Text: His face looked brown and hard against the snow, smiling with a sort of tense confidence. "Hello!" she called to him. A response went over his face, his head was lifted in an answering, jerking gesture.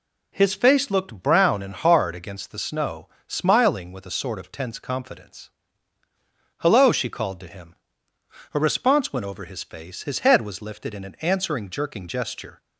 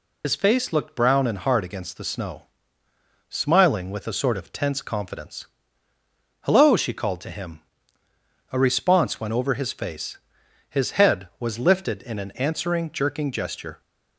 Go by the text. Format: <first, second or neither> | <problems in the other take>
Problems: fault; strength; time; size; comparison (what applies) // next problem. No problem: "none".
first | loses the start of "His"; at 0.2 s; 85 ms